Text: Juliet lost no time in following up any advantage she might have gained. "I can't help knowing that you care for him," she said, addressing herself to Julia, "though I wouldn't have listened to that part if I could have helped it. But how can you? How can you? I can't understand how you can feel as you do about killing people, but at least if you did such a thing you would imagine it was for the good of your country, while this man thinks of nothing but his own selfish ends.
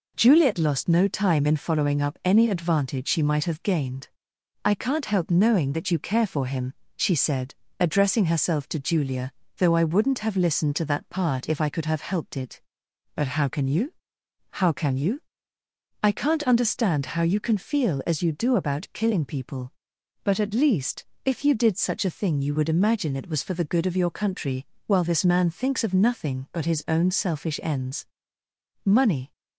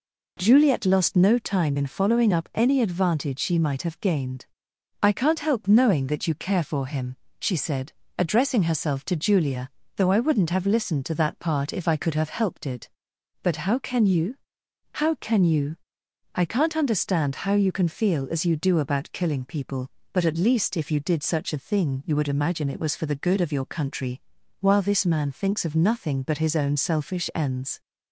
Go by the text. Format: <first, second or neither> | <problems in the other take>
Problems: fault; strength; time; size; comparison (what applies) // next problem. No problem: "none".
second | pauses between "least" and "if"; slight; at 21.0 s; 0.20 s long // goes on to say "Money"; slight; from 28.8 s on; 0.46 s long